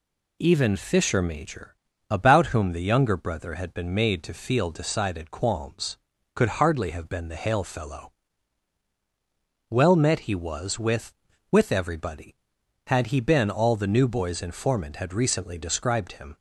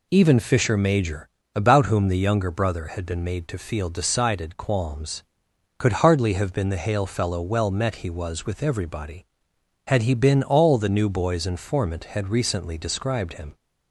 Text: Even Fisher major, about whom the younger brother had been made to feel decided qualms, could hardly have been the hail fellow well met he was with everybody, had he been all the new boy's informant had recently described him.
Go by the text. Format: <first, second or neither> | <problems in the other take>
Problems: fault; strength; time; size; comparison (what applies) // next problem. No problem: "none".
second | pauses between "fellow" and "well"; strong; at 8.1 s; 1.5 s long // says "with" twice; at 11.5 s